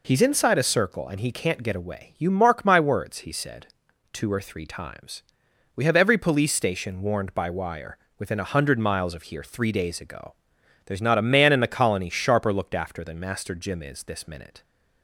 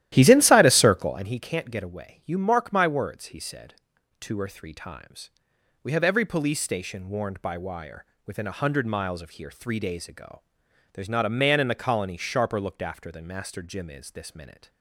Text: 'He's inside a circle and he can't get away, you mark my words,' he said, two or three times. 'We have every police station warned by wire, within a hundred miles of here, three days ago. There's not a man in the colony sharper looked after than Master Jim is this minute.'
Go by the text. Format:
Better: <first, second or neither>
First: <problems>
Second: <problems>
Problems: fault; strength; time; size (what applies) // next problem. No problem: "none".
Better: first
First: none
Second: starts louder than the rest; strong; until 1.4 s; 13.5 dB